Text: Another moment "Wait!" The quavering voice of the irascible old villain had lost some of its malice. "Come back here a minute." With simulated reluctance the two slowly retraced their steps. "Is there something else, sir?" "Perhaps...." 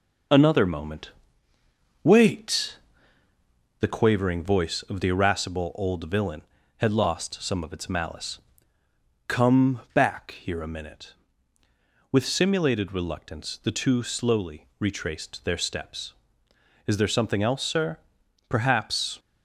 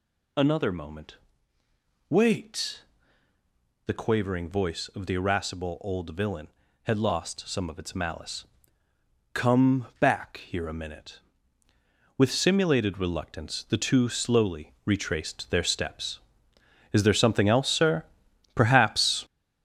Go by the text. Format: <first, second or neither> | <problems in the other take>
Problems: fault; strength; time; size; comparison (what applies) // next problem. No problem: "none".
first | gets louder; strong; throughout; 7.5 dB // pauses between "moment" and "Wait"; noticeable; at 1.1 s; 0.92 s long; noticeable in the first